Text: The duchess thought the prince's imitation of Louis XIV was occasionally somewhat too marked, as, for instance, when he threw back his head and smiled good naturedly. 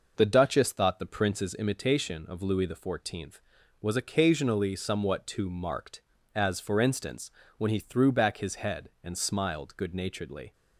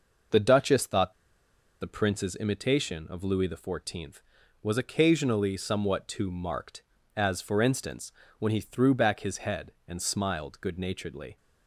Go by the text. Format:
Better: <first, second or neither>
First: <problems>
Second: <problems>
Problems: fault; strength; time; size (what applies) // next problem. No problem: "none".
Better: first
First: none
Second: pauses between "thought" and "the"; noticeable; at 1.1 s; 0.67 s long